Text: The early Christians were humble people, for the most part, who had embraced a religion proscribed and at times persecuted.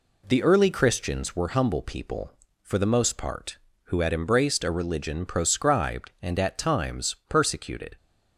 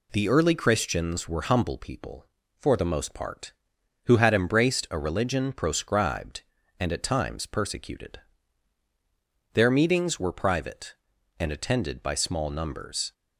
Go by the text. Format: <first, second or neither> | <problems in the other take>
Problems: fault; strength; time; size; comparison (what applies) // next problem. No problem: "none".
first | goes on to say "Their meetings were private and attended by small numbers"; strong; from 9.5 s on; 3.6 s long